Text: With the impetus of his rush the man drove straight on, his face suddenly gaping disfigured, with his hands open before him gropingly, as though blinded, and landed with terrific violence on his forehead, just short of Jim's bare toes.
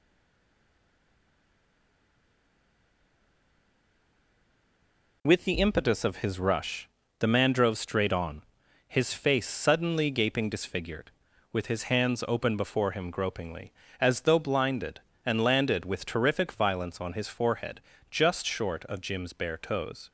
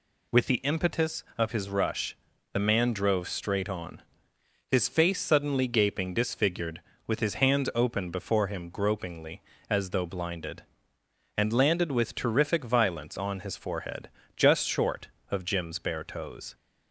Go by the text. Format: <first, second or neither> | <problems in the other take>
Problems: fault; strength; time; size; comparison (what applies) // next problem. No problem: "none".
second | stays silent before the first word; strong; until 5.2 s; 5.2 s long // pauses between "rush" and "the"; slight; at 6.8 s; 0.30 s long; also in the second